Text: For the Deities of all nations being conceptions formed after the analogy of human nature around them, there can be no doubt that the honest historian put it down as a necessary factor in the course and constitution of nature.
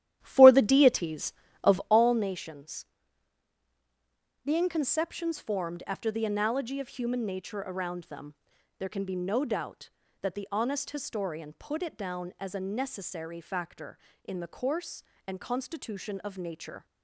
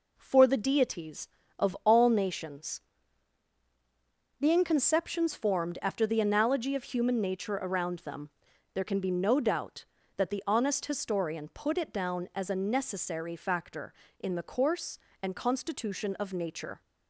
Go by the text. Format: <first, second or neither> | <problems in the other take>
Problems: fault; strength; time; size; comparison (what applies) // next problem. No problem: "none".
second | starts louder than the rest; strong; until 2.1 s; 12 dB // pauses between "nations" and "being"; strong; at 2.8 s; 1.5 s long; strong in the second